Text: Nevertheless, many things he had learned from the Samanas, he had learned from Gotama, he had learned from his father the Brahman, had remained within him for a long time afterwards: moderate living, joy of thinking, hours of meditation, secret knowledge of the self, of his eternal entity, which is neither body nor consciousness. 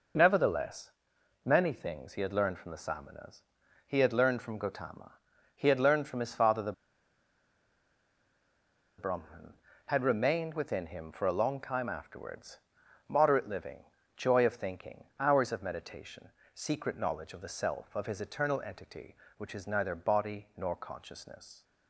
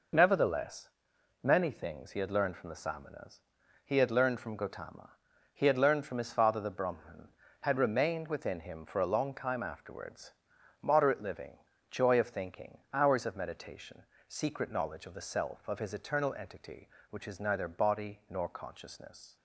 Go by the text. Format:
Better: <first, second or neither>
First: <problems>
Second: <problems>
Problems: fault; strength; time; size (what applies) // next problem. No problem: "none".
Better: second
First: pauses between "the" and "Brahman"; strong; at 6.7 s; 2.2 s long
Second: none